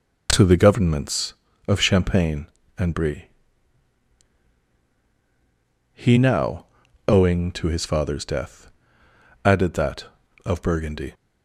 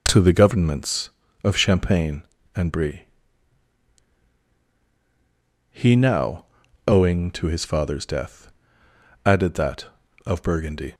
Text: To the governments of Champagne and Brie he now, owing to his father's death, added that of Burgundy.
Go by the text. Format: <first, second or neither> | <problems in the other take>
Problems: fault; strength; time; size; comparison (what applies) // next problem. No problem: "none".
neither | pauses between "Brie" and "he"; strong; the same in both